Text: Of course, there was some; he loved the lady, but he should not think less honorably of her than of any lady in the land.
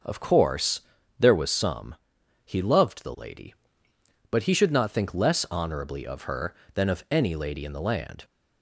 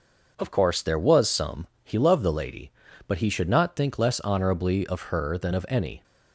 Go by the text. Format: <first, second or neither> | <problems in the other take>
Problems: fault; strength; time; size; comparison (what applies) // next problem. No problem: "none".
first | starts louder than the rest; noticeable; until 1.3 s; 6 dB; also in the first // stops before "lady in the land"; at 6.0 s